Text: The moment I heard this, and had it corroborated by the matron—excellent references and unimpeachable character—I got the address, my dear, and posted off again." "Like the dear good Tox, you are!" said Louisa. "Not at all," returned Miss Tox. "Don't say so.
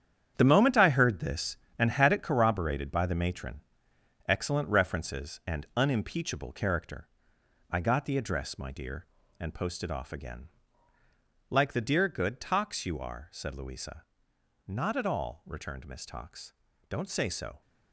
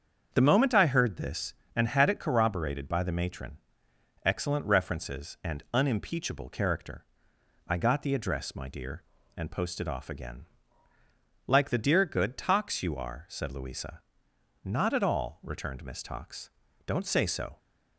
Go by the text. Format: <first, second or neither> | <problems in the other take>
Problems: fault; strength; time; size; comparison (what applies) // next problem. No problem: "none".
second | gets quieter; strong; throughout; 10.5 dB // starts louder than the rest; strong; until 1.3 s; 9 dB; strong in the second